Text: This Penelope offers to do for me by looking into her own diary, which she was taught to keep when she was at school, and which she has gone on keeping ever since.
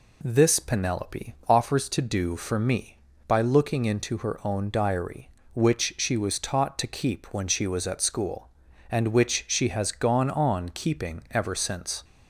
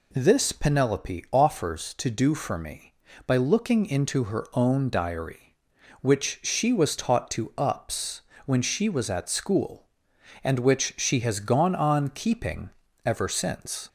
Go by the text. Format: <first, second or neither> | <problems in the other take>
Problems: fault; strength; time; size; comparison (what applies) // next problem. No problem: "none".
first | says "ups" for "keep"; at 7.5 s // pauses between "keeping" and "ever"; at 12.6 s; 0.38 s long